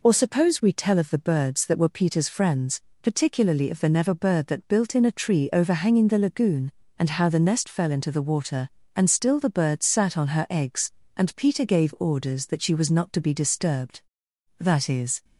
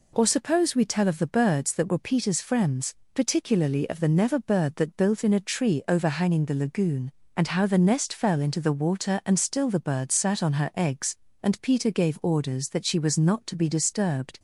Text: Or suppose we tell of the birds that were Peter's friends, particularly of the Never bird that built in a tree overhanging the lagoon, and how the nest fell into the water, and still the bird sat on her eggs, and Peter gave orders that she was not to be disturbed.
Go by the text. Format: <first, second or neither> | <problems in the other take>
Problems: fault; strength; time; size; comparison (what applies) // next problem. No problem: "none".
second | goes on to say "That is"; noticeable; from 14.5 s on; 0.66 s long